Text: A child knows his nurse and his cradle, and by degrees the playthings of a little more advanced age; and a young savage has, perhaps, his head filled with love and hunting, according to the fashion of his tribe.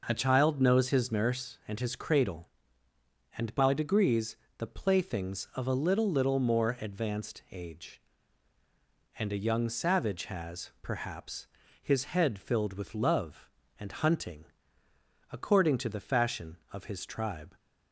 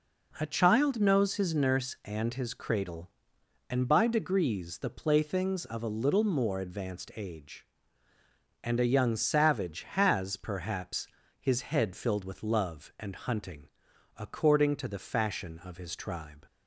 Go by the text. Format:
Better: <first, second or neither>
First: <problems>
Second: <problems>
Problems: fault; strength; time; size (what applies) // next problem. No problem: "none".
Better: second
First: pauses between "degrees" and "the"; slight; at 4.3 s; 0.22 s long // says "little" twice; at 6.0 s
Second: none